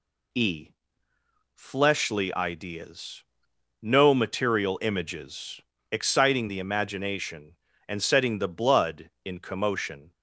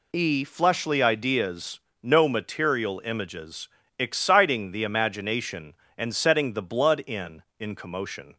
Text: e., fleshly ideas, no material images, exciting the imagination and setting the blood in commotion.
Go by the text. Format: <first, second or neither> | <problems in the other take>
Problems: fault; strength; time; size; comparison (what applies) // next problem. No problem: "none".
first | says "in" twice; at 7.5 s